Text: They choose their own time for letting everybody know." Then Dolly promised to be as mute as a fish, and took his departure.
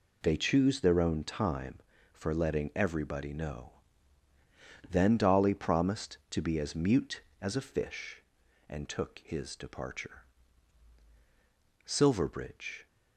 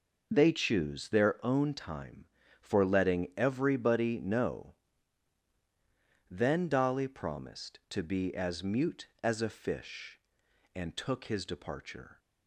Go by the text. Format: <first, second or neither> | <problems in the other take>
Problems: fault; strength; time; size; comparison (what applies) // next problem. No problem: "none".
second | goes on to say "Silverbridge"; noticeable; from 11.8 s on; 1.0 s long